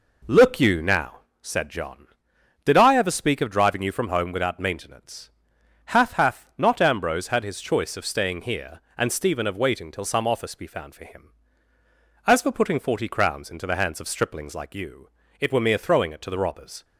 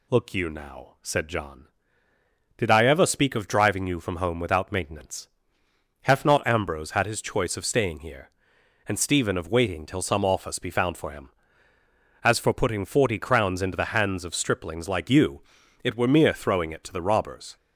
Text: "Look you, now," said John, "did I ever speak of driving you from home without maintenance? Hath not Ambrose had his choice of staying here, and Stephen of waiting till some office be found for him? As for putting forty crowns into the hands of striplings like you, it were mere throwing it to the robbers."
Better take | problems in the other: second | says "Hath" twice; at 6.1 s

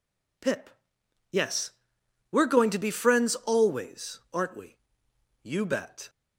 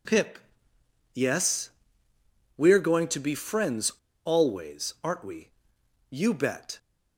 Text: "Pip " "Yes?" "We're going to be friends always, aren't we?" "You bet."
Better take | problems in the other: first | pauses between "friends" and "always"; slight; at 3.9 s; 0.35 s long

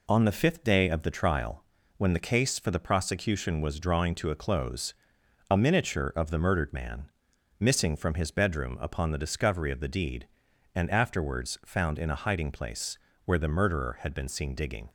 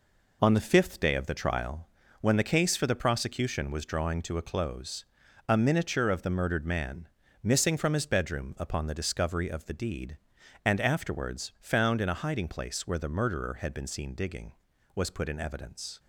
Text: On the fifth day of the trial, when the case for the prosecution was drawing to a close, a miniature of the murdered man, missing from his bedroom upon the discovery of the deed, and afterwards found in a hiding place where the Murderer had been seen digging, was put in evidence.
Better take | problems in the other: second | pauses between "place" and "where"; slight; at 12.9 s; 0.26 s long // stops before "was put in evidence"; at 14.8 s

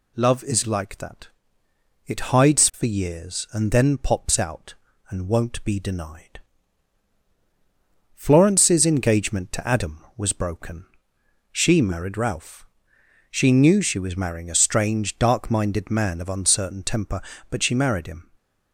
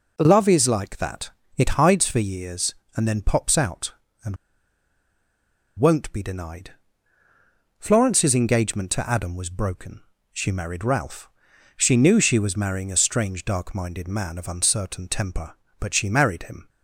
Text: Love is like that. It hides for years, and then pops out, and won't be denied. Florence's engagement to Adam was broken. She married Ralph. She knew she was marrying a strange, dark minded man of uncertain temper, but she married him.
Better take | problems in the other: first | pauses between "and" and "won't"; strong; at 4.3 s; 1.4 s long

